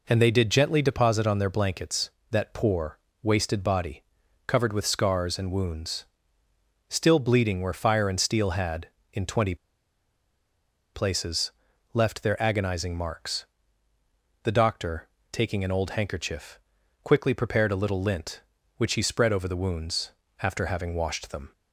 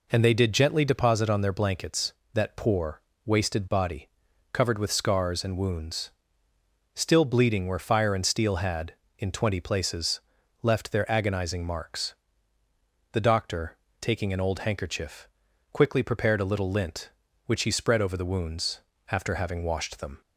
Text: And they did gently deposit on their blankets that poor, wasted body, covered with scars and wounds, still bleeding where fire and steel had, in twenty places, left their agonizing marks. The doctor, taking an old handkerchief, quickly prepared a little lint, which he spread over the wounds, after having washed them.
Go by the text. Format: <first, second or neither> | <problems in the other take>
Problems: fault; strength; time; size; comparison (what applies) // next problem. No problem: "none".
second | pauses between "twenty" and "places"; strong; at 9.5 s; 1.3 s long